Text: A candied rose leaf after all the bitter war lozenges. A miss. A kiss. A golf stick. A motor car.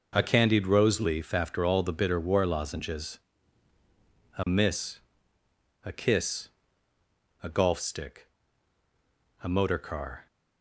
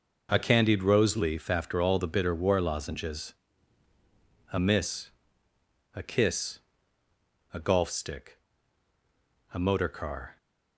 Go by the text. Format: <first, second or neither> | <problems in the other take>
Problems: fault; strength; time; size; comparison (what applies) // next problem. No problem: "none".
neither | none